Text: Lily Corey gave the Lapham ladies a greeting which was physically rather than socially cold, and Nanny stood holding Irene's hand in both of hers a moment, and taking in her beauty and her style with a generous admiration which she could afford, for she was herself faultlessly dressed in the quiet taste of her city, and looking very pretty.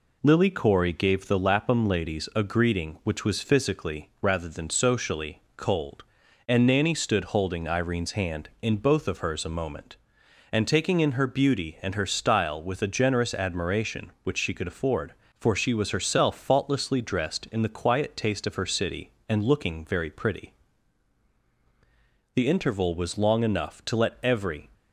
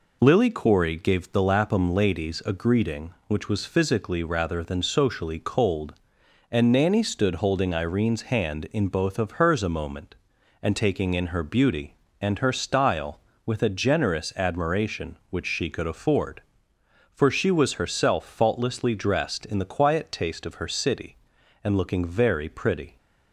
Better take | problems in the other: second | goes on to say "The interval was long enough to let every"; strong; from 22.3 s on; 2.3 s long

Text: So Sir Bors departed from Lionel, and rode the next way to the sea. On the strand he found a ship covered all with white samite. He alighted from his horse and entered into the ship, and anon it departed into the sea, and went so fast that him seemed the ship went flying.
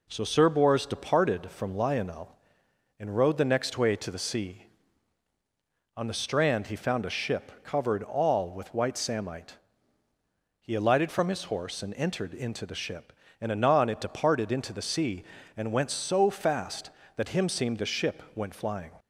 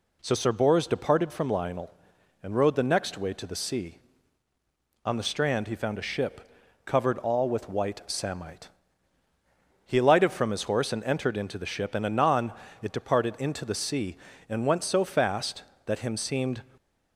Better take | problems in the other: first | pauses between "ship" and "covered"; at 6.4 s; 0.38 s long // pauses between "anon" and "it"; slight; at 12.5 s; 0.28 s long // stops before "the ship went flying"; at 16.7 s

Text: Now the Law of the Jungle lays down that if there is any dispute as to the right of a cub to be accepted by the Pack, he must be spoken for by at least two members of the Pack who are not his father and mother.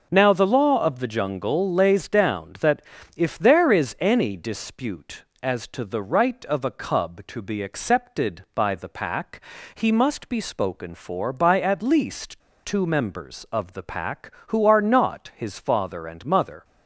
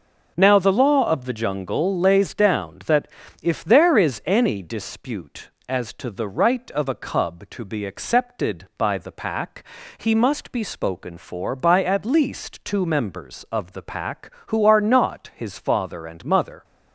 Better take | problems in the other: second | starts louder than the rest; until 1.1 s; 6 dB; also in the second // pauses between "that" and "if"; slight; at 2.8 s; 0.36 s long; slight in the second // pauses between "least" and "two"; slight; at 12.4 s; 0.24 s long

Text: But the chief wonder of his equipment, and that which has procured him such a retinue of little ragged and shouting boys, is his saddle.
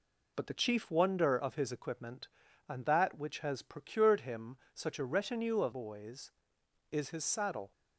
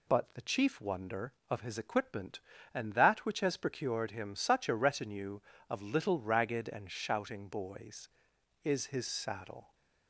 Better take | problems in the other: second | pauses between "him" and "such"; slight; at 4.5 s; 0.16 s long // skips "little ragged and shouting"; at 5.7 s

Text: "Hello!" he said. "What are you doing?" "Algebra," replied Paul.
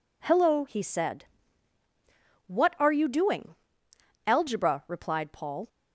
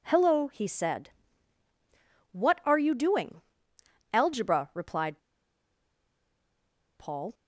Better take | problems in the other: first | pauses between "replied" and "Paul"; strong; at 5.1 s; 1.7 s long

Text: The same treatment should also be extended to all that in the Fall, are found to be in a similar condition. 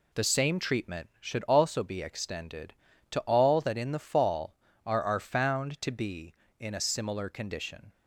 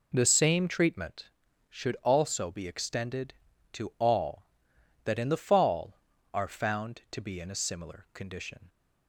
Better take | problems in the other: second | says "are" twice; at 5.0 s

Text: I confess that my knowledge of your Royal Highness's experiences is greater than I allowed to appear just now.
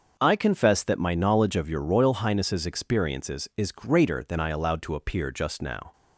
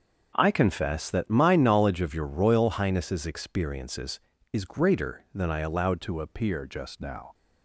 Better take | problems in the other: first | starts louder than the rest; until 1.3 s; 6.5 dB; also in the first // changes voice at "to"; from 6.0 s on; 1.3 s long

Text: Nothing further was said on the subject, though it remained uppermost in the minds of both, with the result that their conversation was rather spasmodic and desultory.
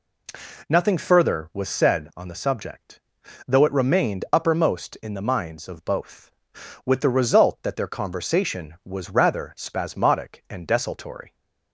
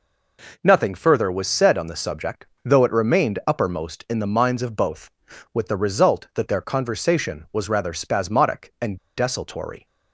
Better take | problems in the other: first | pauses between "and" and "desultory"; slight; at 8.9 s; 0.20 s long

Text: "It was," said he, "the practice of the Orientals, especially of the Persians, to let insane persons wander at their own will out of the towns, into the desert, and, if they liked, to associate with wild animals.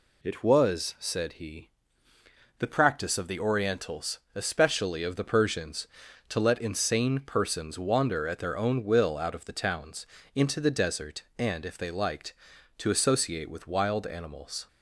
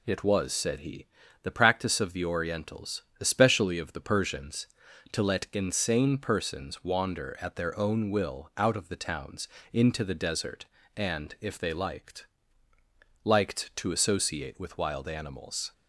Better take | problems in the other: first | says "liked" twice; at 13.2 s

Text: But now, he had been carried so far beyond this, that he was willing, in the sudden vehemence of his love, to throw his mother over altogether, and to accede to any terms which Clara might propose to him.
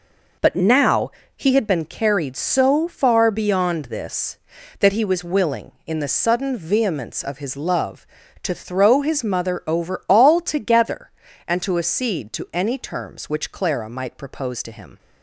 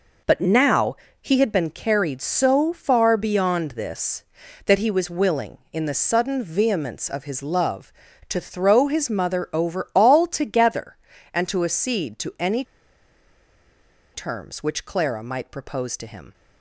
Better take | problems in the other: first | pauses between "any" and "terms"; strong; at 12.6 s; 1.4 s long

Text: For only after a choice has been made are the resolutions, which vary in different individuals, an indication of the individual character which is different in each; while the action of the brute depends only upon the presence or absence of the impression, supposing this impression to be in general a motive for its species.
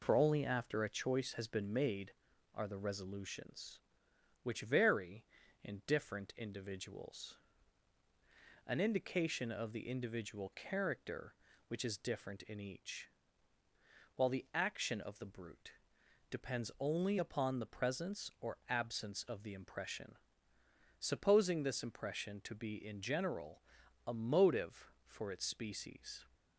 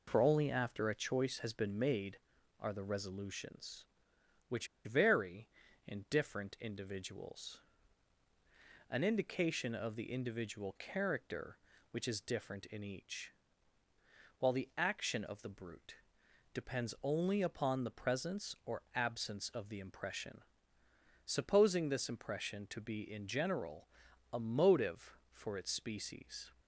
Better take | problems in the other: first | pauses between "which" and "vary"; slight; at 4.6 s; 0.19 s long // pauses between "brute" and "depends"; noticeable; at 15.9 s; 0.60 s long; noticeable in the first // pauses between "general" and "a"; noticeable; at 23.8 s; 0.46 s long; noticeable in the first

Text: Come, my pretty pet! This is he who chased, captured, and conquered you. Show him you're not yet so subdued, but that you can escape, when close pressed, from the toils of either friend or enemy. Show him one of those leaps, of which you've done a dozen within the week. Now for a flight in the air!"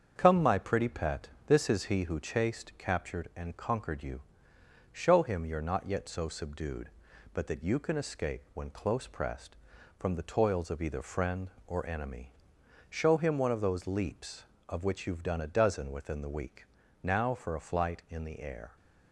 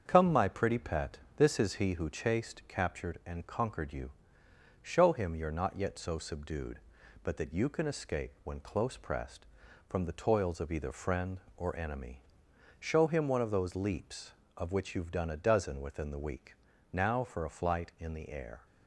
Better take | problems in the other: neither | starts louder than the rest; strong; the same in both

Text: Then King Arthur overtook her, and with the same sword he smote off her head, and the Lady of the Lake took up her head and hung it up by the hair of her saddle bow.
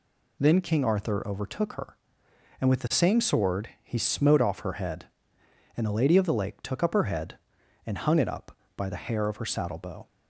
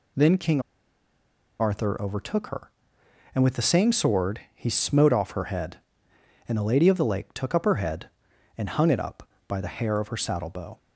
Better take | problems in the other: first | pauses between "King" and "Arthur"; at 0.6 s; 0.99 s long

